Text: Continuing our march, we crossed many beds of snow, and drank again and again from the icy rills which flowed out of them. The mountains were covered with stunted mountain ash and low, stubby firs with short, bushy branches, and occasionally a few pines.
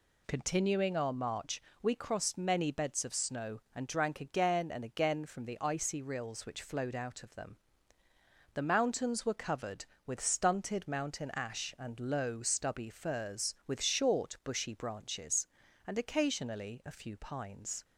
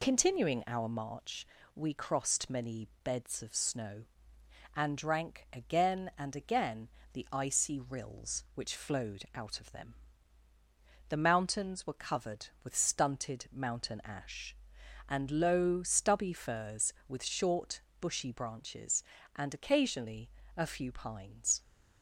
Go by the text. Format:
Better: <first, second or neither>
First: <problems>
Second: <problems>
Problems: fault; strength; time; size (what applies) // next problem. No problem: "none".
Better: first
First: none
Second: pauses between "many" and "beds"; slight; at 2.8 s; 0.16 s long // skips "from"; at 7.0 s // pauses between "occasionally" and "a"; slight; at 20.2 s; 0.28 s long